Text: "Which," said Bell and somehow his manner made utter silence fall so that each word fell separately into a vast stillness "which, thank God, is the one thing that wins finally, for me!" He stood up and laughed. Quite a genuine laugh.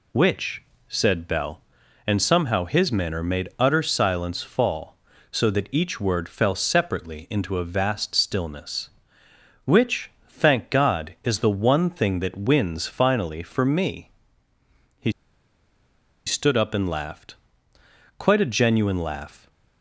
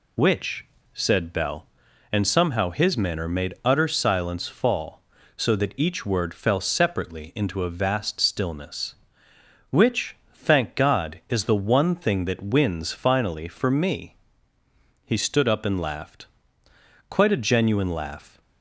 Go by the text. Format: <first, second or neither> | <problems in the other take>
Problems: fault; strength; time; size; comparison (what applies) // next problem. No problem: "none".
second | pauses between "He" and "stood"; at 15.1 s; 1.1 s long